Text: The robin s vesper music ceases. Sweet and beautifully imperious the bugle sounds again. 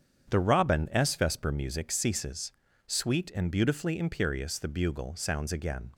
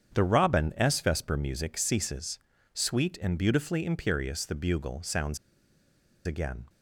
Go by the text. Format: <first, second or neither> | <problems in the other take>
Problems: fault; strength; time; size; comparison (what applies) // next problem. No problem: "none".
first | starts louder than the rest; strong; until 1.1 s; 8.5 dB; strong in the first // pauses between "sounds" and "again"; noticeable; at 5.3 s; 0.88 s long